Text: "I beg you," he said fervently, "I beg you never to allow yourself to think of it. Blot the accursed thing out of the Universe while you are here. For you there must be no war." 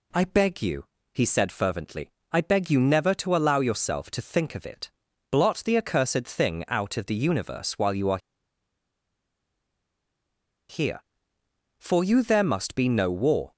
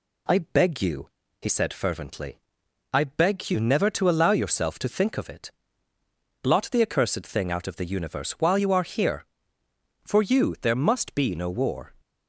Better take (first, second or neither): second